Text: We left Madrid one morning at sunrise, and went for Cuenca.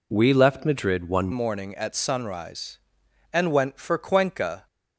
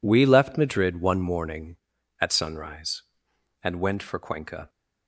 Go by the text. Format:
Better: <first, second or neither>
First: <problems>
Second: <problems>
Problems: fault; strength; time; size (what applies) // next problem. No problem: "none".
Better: second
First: changes voice at "morning"; from 1.3 s on; 3.3 s long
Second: none